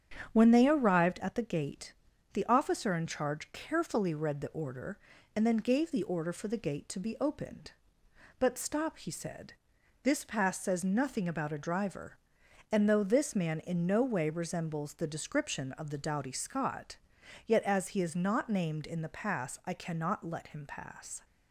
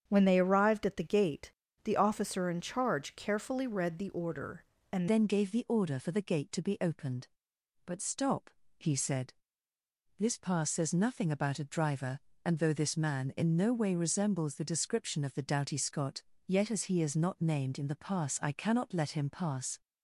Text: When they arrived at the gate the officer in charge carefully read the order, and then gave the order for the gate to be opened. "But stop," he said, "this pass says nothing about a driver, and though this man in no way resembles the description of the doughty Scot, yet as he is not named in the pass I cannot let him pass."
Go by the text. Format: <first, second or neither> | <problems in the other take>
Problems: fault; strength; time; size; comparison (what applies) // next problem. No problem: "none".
first | starts louder than the rest; strong; until 1.0 s; 8 dB; strong in the first // pauses between "gate" and "the"; slight; at 1.5 s; 0.32 s long; also in the first // changes voice at "then"; from 5.0 s on; 14.8 s long